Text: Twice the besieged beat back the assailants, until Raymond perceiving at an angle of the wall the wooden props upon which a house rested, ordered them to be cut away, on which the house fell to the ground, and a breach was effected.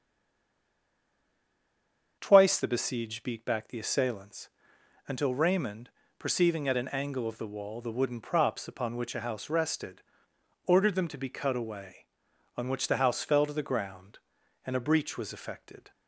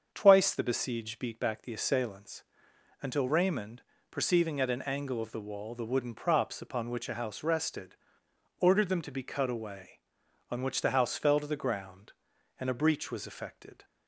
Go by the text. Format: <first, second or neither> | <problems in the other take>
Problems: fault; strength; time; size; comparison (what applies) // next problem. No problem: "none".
second | stays silent before the first word; until 2.1 s; 2.1 s long // starts louder than the rest; until 3.2 s; 7 dB; also in the second // pauses between "Raymond" and "perceiving"; slight; at 5.8 s; 0.28 s long; slight in the second